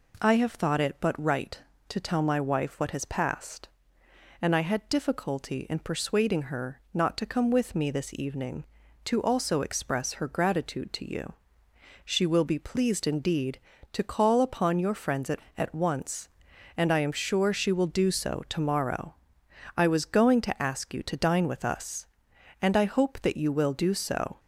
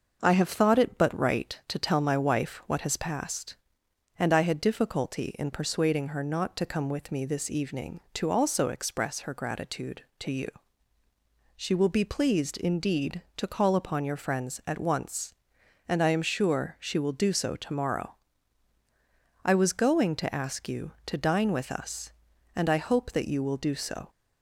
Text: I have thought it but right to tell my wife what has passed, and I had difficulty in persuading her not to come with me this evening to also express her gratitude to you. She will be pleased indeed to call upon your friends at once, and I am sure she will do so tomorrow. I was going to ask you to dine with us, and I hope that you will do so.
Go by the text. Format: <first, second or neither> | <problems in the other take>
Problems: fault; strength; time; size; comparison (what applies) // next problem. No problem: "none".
second | says "at" twice; at 15.5 s